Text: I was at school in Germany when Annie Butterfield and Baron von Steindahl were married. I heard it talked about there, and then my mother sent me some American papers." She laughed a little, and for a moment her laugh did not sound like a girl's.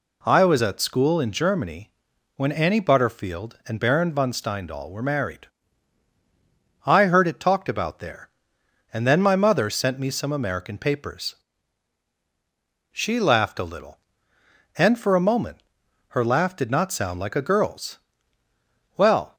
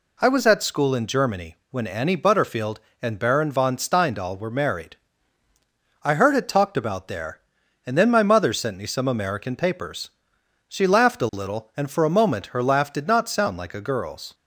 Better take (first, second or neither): second